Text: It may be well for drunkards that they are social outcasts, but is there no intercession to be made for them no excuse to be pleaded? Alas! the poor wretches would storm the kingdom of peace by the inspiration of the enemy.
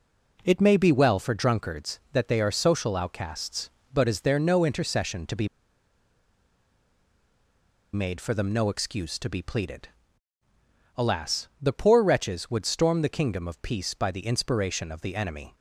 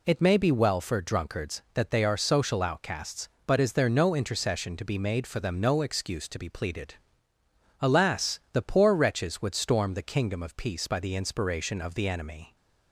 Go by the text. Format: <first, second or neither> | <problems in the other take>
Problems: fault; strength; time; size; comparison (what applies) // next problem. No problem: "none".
second | pauses between "be" and "made"; strong; at 5.4 s; 2.4 s long